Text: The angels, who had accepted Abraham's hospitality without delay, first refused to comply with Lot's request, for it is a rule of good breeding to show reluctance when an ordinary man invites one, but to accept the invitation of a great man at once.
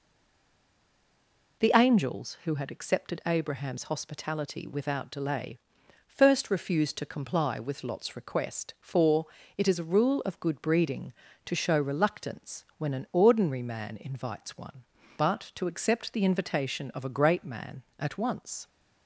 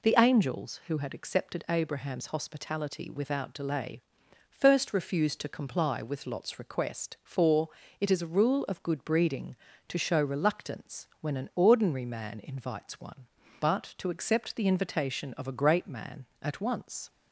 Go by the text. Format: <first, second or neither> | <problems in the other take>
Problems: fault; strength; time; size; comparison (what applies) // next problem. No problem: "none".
second | stays silent before the first word; noticeable; until 1.5 s; 1.5 s long // pauses between "for" and "it"; slight; at 9.2 s; 0.30 s long; slight in the second